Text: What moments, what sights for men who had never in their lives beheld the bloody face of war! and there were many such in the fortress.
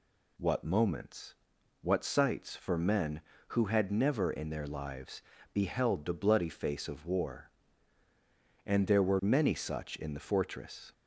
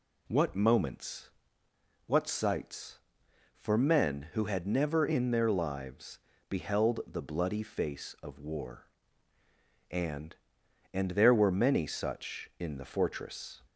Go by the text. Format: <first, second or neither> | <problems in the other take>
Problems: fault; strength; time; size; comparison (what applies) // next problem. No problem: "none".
first | pauses between "lives" and "beheld"; slight; at 6.1 s; 0.30 s long; slight in the first // says "and" twice; at 10.9 s